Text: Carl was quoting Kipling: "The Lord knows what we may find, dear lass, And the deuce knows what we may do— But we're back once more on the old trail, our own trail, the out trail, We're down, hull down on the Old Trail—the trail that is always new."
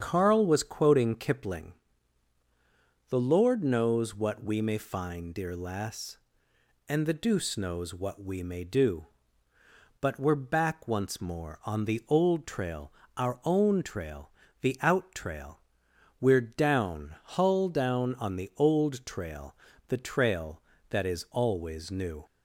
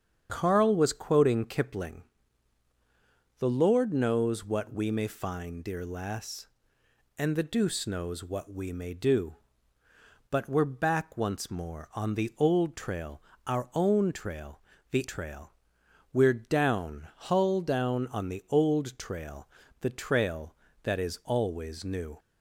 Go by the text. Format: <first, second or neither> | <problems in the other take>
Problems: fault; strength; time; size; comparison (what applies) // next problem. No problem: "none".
first | starts louder than the rest; strong; until 1.3 s; 8 dB; strong in the first // skips "out"; at 15.0 s